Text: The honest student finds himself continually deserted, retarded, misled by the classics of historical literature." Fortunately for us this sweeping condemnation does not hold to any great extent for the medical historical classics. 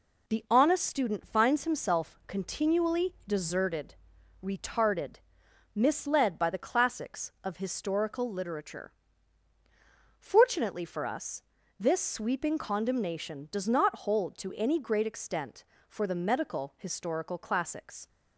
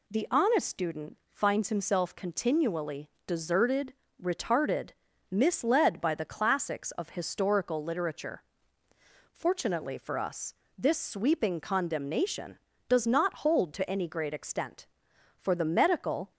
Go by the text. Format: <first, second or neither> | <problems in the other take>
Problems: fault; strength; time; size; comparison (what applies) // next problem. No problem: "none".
first | pauses between "student" and "finds"; slight; at 1.1 s; 0.16 s long // pauses between "continually" and "deserted"; slight; at 3.0 s; 0.18 s long // pauses between "us" and "this"; slight; at 10.5 s; 0.26 s long; slight in the first // stops before "historical classics"; at 16.3 s